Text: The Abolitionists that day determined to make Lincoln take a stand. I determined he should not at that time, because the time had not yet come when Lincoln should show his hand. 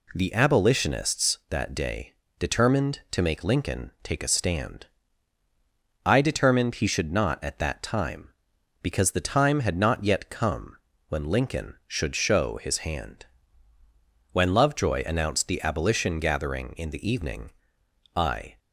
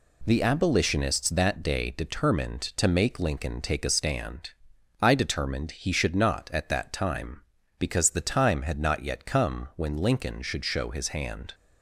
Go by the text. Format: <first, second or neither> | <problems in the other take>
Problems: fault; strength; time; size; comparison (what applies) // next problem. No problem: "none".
second | pauses between "day" and "determined"; slight; at 2.1 s; 0.26 s long // pauses between "come" and "when"; slight; at 10.7 s; 0.32 s long // goes on to say "When Lovejoy announced the Abolition gathering in the evening I"; strong; from 14.3 s on; 4.2 s long